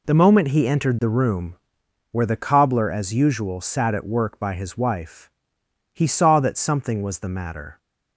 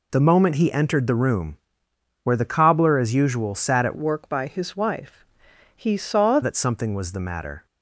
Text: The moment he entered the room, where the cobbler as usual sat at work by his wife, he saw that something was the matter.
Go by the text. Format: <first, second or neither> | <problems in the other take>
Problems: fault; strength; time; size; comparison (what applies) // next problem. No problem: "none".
first | changes voice from "work" to "saw"; from 3.9 to 6.4 s; 2.5 s long